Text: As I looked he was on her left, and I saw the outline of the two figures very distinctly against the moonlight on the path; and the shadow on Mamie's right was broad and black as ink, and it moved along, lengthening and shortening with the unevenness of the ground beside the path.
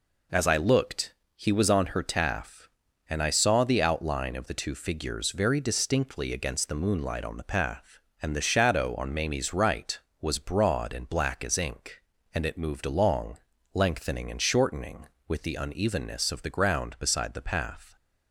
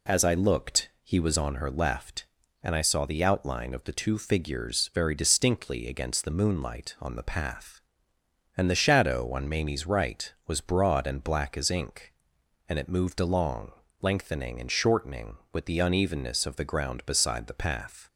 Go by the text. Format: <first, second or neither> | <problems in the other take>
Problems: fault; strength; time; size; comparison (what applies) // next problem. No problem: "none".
second | pauses between "looked" and "he"; slight; at 1.1 s; 0.22 s long // says "taff" for "left"; at 2.0 s